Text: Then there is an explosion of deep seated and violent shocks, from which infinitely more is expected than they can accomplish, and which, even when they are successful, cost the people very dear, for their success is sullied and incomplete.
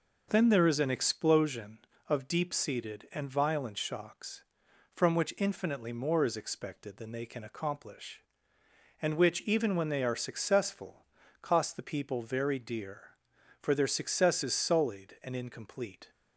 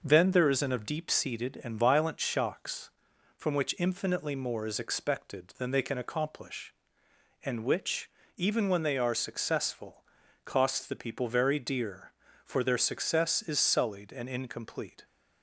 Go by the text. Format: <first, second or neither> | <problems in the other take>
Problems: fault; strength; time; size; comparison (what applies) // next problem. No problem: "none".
first | skips "explosion"; at 0.7 s